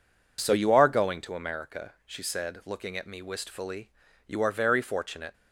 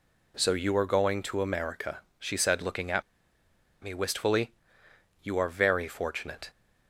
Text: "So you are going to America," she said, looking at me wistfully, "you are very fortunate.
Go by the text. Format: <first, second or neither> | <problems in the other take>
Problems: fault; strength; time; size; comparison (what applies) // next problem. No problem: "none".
first | pauses between "at" and "me"; noticeable; at 3.0 s; 0.81 s long